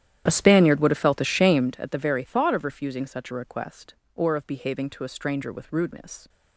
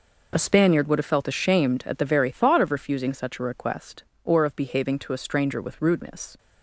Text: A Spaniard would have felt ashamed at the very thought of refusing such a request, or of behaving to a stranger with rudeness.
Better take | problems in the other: second | starts louder than the rest; strong; until 1.8 s; 11 dB

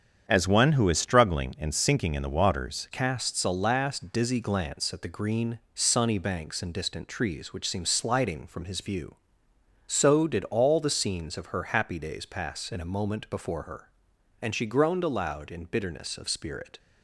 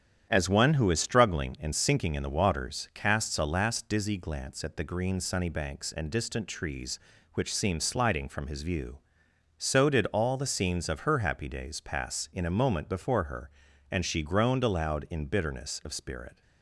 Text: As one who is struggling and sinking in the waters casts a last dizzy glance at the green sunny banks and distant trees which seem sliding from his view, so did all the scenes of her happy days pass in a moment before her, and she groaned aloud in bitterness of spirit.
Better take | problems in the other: second | starts louder than the rest; strong; until 1.2 s; 8 dB; strong in the second // changes voice at "casts"; from 2.9 s on; 13.8 s long // pauses between "green" and "sunny"; slight; at 5.5 s; 0.16 s long

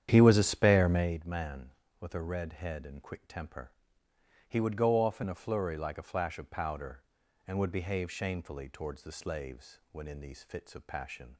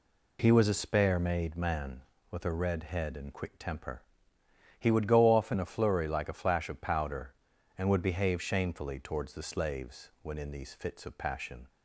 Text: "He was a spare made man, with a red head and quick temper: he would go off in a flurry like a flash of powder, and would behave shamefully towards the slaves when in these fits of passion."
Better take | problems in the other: second | starts louder than the rest; strong; until 1.2 s; 9.5 dB

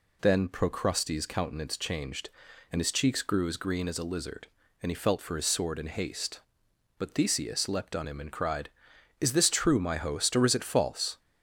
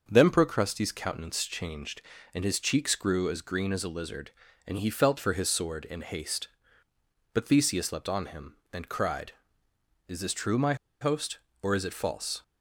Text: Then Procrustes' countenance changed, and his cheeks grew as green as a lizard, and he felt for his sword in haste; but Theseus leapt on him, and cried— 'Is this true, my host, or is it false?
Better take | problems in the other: first | starts louder than the rest; until 1.0 s; 6.5 dB // pauses between "my" and "host"; slight; at 10.7 s; 0.25 s long

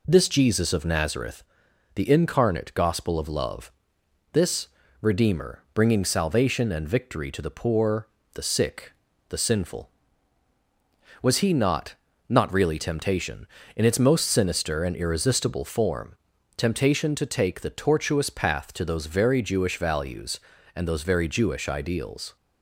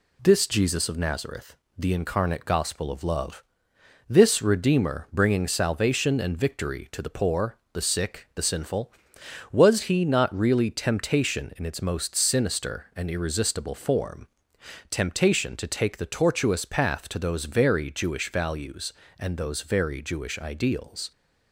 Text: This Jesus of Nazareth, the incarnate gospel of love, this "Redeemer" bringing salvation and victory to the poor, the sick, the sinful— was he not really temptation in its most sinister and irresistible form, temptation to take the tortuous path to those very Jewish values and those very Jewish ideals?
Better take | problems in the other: second | pauses between "this" and "Redeemer"; slight; at 4.6 s; 0.34 s long // says "not" twice; at 12.2 s

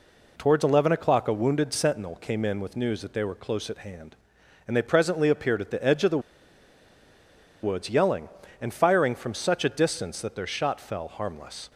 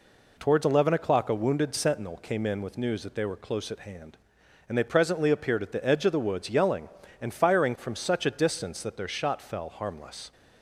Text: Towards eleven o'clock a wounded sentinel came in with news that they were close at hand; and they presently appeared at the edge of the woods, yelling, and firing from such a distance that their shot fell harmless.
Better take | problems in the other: second | pauses between "the" and "woods"; strong; at 6.1 s; 1.4 s long

